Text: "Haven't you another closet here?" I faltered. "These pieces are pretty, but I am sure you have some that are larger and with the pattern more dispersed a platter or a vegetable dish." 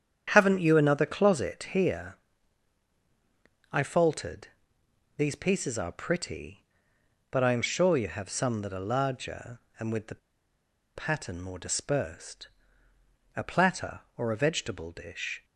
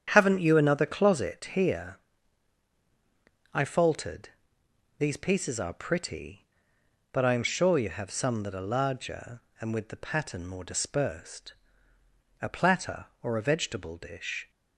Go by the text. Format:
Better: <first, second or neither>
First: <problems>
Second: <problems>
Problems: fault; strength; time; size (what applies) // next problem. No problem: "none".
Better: second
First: starts louder than the rest; strong; until 1.3 s; 8.5 dB // pauses between "the" and "pattern"; noticeable; at 10.1 s; 0.77 s long // pauses between "dispersed" and "a"; noticeable; at 12.4 s; 0.88 s long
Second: starts louder than the rest; strong; until 1.1 s; 9 dB // pauses between "dispersed" and "a"; noticeable; at 11.5 s; 0.88 s long